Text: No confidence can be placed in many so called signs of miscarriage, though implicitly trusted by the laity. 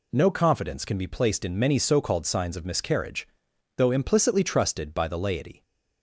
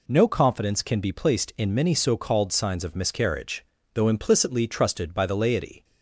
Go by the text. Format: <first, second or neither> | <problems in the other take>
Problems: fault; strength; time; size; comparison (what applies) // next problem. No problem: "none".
neither | none